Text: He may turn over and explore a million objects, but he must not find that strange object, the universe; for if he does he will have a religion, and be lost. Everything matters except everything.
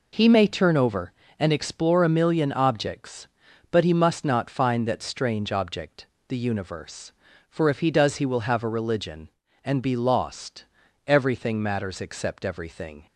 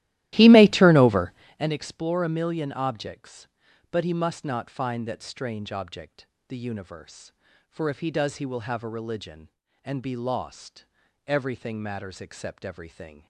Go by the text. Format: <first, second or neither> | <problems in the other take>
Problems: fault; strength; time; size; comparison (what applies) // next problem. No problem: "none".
first | starts louder than the rest; strong; until 1.7 s; 15 dB